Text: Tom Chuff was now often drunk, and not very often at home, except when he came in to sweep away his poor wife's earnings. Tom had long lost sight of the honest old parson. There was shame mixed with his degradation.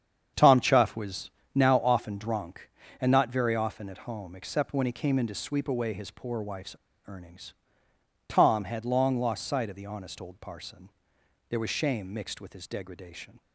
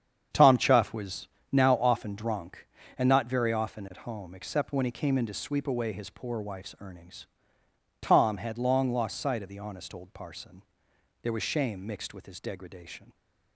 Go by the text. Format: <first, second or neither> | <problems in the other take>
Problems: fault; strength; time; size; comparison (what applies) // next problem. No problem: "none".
second | starts louder than the rest; strong; until 1.5 s; 8 dB; strong in the second // pauses between "was" and "now"; slight; at 1.3 s; 0.22 s long; slight in the second // pauses between "wife's" and "earnings"; slight; at 6.7 s; 0.32 s long